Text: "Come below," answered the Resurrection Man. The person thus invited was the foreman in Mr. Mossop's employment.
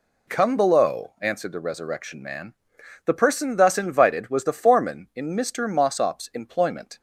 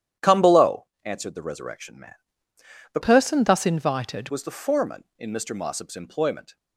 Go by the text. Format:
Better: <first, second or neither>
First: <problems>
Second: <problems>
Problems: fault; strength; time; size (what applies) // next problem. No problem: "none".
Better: first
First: none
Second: starts louder than the rest; strong; until 1.3 s; 10.5 dB // changes voice from "person" to "invited"; from 3.0 to 4.2 s; 1.2 s long